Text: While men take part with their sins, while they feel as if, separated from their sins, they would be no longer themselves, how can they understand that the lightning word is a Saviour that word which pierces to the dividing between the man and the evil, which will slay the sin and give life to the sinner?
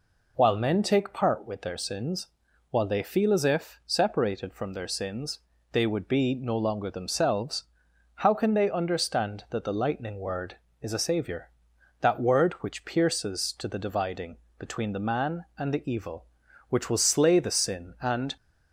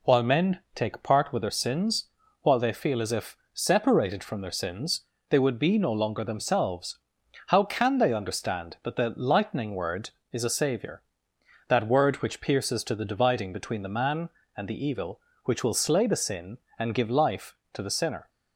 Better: second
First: pauses between "dividing" and "between"; slight; at 14.3 s; 0.24 s long // stops before "give life to the sinner"; at 18.3 s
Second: none

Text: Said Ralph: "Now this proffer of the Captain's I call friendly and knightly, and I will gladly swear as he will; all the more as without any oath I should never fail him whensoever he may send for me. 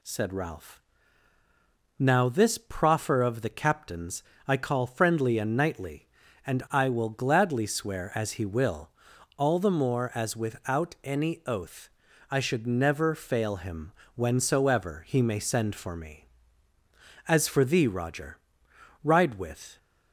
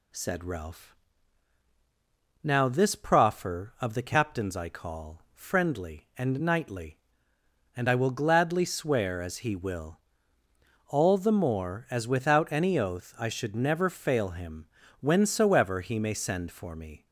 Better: second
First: pauses between "Captain's" and "I"; slight; at 4.2 s; 0.24 s long // pauses between "oath" and "I"; at 11.8 s; 0.42 s long // pauses between "him" and "whensoever"; slight; at 13.9 s; 0.24 s long // goes on to say "As for thee Roger ride with"; strong; from 17.2 s on; 2.5 s long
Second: pauses between "him" and "whensoever"; slight; at 14.6 s; 0.34 s long

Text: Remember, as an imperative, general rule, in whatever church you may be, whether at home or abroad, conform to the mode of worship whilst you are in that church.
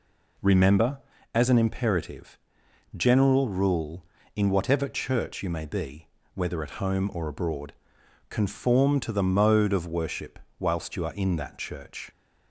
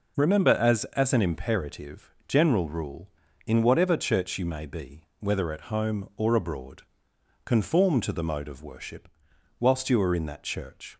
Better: first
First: pauses between "worship" and "whilst"; slight; at 10.3 s; 0.20 s long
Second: says "as" twice; at 0.9 s // pauses between "worship" and "whilst"; noticeable; at 9.0 s; 0.50 s long

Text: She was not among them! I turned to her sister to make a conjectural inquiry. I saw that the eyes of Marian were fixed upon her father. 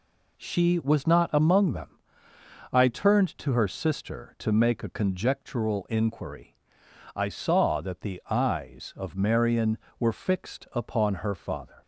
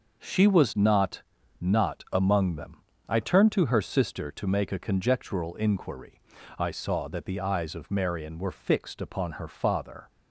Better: first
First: none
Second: says "not" twice; at 1.5 s

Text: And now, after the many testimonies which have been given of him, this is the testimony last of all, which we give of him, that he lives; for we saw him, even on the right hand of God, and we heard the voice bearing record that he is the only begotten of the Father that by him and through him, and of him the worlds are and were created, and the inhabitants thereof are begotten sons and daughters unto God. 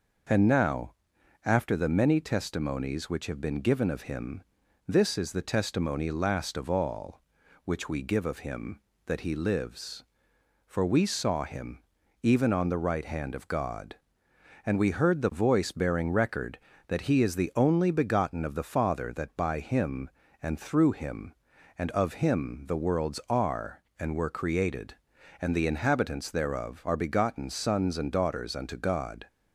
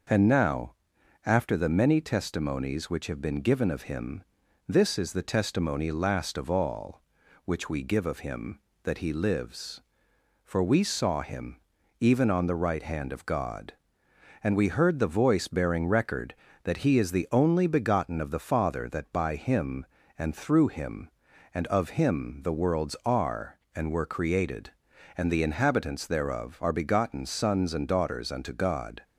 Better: neither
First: none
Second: none

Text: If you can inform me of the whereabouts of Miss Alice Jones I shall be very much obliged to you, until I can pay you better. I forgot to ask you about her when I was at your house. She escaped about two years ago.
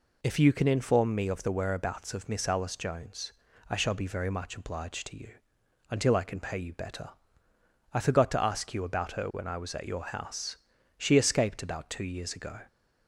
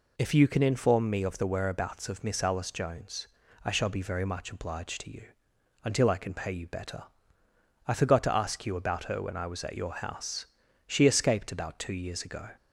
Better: neither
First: pauses between "Jones" and "I"; at 3.3 s; 0.38 s long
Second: pauses between "Jones" and "I"; at 3.2 s; 0.38 s long

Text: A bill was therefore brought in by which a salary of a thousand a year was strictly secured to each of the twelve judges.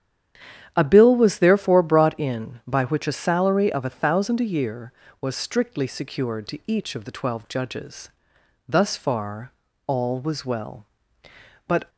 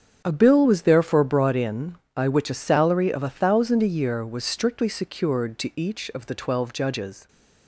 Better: second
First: starts louder than the rest; strong; until 1.7 s; 10 dB // goes on to say "Thus far all was well But"; strong; from 8.6 s on; 3.2 s long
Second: starts louder than the rest; strong; until 1.2 s; 8 dB

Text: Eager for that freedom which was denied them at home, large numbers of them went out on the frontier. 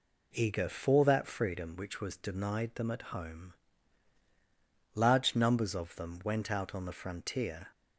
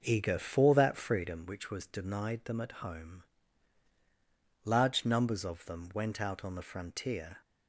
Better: first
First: none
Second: starts louder than the rest; noticeable; until 1.5 s; 6 dB

